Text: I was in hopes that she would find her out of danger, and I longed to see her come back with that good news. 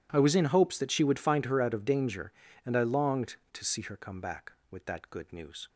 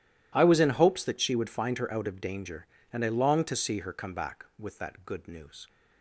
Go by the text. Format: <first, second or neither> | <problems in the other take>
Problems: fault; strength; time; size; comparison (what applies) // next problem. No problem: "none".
neither | none